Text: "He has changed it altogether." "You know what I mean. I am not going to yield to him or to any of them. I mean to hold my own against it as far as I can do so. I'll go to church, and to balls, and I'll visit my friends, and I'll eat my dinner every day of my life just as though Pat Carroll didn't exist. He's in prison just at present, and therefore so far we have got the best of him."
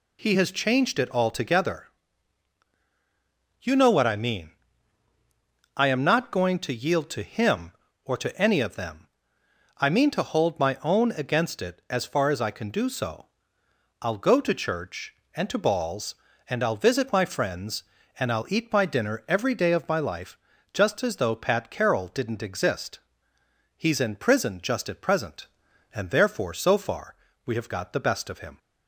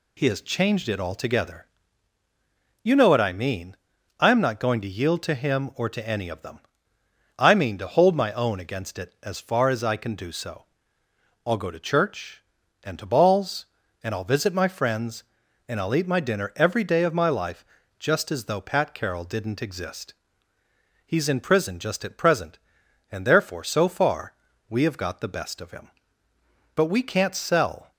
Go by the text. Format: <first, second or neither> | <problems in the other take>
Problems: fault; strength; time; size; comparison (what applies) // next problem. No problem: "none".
first | pauses between "life" and "just"; slight; at 17.6 s; 0.34 s long; also in the first // pauses between "far" and "we"; slight; at 24.3 s; 0.36 s long; slight in the first // goes on to say "But we can't sell"; noticeable; from 26.7 s on; 1.1 s long